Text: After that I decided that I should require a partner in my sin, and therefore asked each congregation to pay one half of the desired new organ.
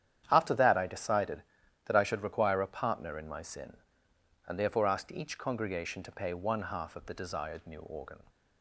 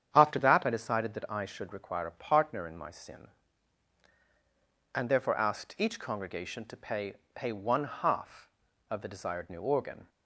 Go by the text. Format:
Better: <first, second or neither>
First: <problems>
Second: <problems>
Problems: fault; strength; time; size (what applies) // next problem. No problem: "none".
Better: first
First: starts louder than the rest; strong; until 1.3 s; 9.5 dB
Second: starts louder than the rest; strong; until 1.1 s; 8.5 dB // says "pay" twice; at 7.3 s